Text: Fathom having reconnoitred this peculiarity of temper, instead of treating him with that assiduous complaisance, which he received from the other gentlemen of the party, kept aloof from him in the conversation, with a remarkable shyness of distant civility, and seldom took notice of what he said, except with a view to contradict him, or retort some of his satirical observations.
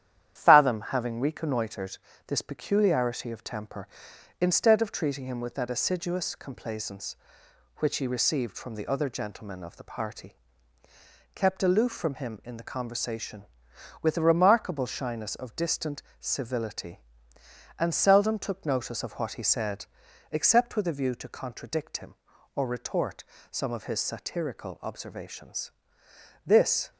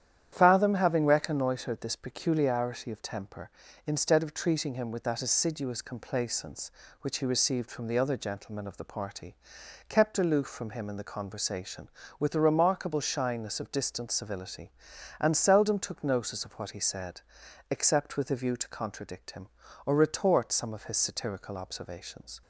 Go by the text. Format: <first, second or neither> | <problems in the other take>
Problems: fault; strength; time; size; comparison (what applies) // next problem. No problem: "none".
second | starts louder than the rest; strong; until 1.3 s; 10.5 dB; strong in the second // pauses between "reconnoitred" and "this"; slight; at 1.9 s; 0.30 s long // pauses between "distant" and "civility"; slight; at 16.0 s; 0.18 s long // pauses between "retort" and "some"; slight; at 23.2 s; 0.26 s long // goes on to say "This"; slight; from 26.4 s on; 0.46 s long